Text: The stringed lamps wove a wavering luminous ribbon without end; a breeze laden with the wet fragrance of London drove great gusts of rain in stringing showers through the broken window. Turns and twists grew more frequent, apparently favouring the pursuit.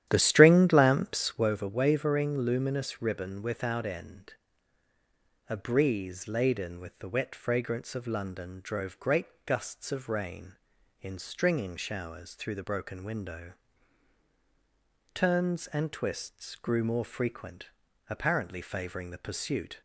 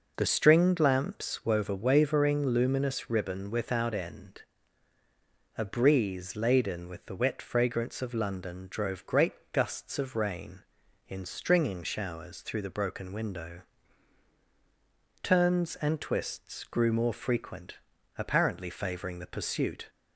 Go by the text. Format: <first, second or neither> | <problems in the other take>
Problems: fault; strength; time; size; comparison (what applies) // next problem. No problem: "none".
second | starts louder than the rest; strong; until 1.6 s; 12 dB